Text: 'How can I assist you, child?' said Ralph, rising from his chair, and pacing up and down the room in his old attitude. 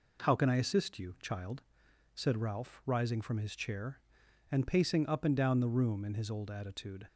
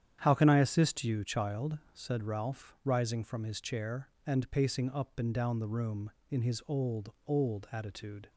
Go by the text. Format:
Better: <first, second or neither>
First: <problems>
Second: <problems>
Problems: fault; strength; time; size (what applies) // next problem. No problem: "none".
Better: first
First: none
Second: starts louder than the rest; strong; until 1.2 s; 9.5 dB // says "old" twice; at 7.2 s